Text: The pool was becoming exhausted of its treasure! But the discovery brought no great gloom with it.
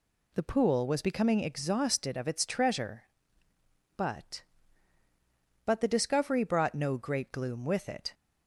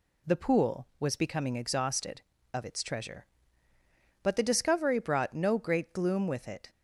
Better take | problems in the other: second | says "But" twice; at 5.6 s

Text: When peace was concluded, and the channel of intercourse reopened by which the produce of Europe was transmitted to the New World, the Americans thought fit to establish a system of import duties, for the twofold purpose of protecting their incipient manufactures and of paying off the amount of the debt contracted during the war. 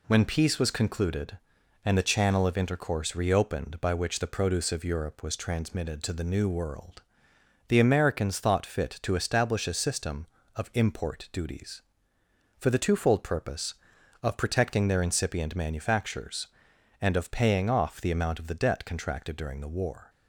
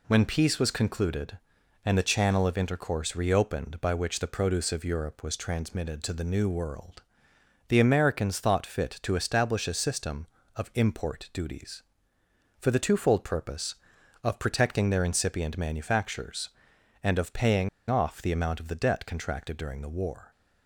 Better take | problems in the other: first | pauses between "paying" and "off"; slight; at 17.6 s; 0.21 s long

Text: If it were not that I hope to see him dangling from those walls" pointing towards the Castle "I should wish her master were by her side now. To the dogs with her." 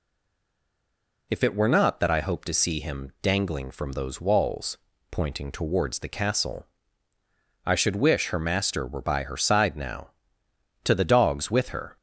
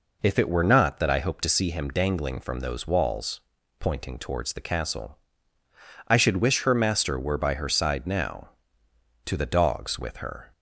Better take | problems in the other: second | stays silent before the first word; noticeable; until 1.3 s; 1.3 s long // pauses between "walls" and "pointing"; slight; at 4.7 s; 0.32 s long; also in the second // pauses between "Castle" and "I"; noticeable; at 6.6 s; 0.98 s long; noticeable in the second

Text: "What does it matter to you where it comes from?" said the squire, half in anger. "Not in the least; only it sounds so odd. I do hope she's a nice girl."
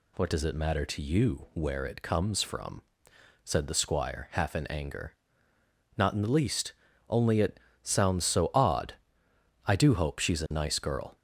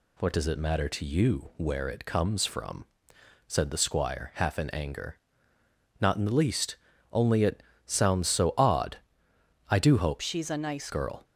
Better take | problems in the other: first | pauses between "it" and "sounds"; slight; at 7.6 s; 0.24 s long; slight in the first // changes voice from "she's" to "nice"; from 10.2 to 10.8 s; 0.6 s long

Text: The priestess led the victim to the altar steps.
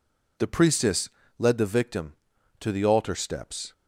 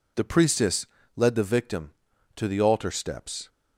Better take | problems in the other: neither | pauses between "priestess" and "led"; slight; the same in both

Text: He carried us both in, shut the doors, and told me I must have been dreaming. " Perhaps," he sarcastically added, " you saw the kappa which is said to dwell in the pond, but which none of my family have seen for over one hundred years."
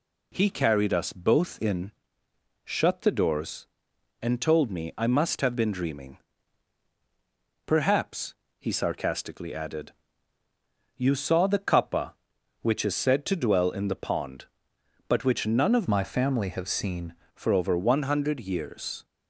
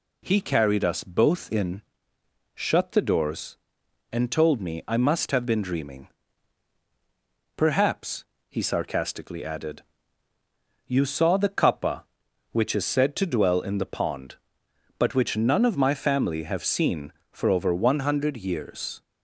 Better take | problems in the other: second | changes voice from "my" to "seen"; from 15.8 to 17.1 s; 1.3 s long

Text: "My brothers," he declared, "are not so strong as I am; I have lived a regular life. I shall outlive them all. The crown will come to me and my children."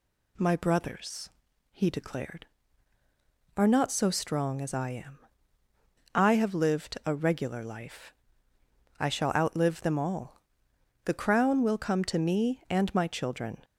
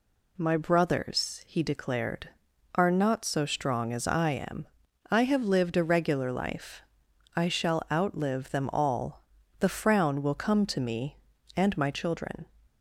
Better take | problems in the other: first | says "frown" for "crown"; at 9.6 s

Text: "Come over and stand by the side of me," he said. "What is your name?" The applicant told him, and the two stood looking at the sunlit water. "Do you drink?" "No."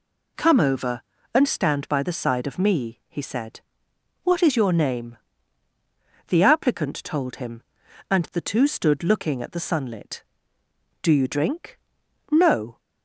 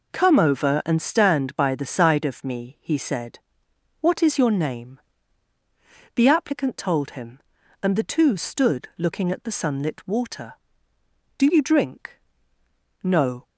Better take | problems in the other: second | skips "water"; at 10.6 s

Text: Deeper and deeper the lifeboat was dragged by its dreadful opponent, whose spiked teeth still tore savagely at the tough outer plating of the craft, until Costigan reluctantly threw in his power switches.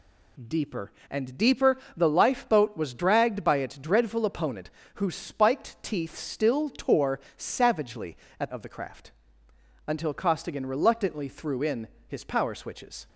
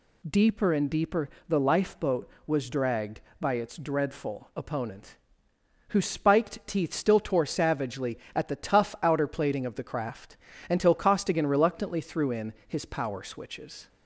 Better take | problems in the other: second | pauses between "deeper" and "the"; slight; at 1.7 s; 0.18 s long; slight in the second // pauses between "tore" and "savagely"; slight; at 7.1 s; 0.18 s long // skips "the tough outer plating"; at 8.5 s // pauses between "in" and "his"; slight; at 11.8 s; 0.18 s long; slight in the second

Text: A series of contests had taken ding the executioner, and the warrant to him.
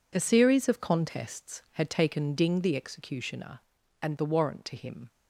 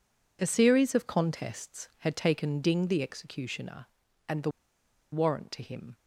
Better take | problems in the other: first | pauses between "the" and "warrant"; noticeable; at 4.4 s; 0.62 s long

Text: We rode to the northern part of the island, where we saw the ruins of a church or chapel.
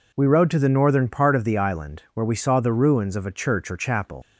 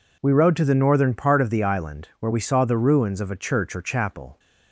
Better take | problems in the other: second | leaves "chapel" unfinished; at 4.2 s; 110 ms

